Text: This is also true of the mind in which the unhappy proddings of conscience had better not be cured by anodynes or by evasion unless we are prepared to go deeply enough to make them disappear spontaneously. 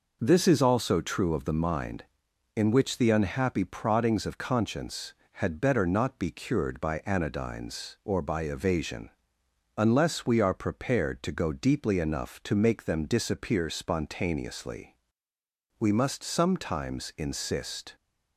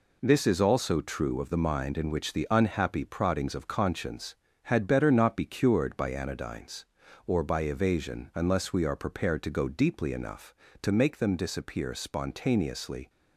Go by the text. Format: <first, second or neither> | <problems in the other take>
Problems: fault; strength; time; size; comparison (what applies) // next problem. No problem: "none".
second | pauses between "evasion" and "unless"; noticeable; at 9.1 s; 0.66 s long // goes on to say "We must sometimes insist"; strong; from 15.7 s on; 2.1 s long